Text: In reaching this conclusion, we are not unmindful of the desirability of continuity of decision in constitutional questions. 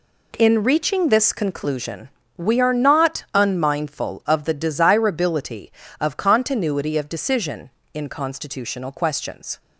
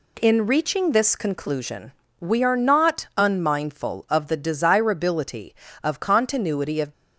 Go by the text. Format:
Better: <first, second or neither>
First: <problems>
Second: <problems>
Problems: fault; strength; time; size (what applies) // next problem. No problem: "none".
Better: first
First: none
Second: stops before "decision in constitutional questions"; at 6.9 s